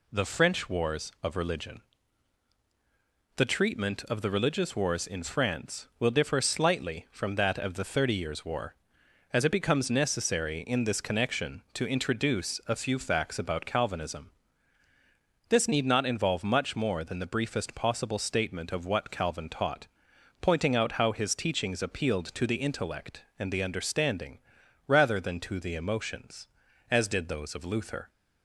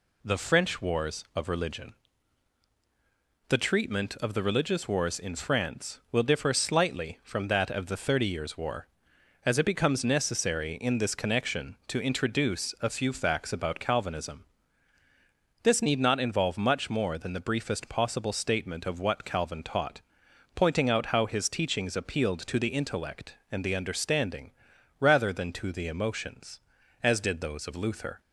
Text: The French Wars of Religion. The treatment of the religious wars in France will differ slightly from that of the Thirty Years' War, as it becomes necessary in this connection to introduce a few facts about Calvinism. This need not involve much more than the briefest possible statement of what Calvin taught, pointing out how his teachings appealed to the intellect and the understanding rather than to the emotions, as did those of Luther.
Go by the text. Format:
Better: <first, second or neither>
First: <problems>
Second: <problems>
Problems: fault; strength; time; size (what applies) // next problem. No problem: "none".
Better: neither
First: pauses between "understanding" and "rather"; noticeable; at 24.3 s; 0.48 s long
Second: pauses between "understanding" and "rather"; noticeable; at 24.5 s; 0.48 s long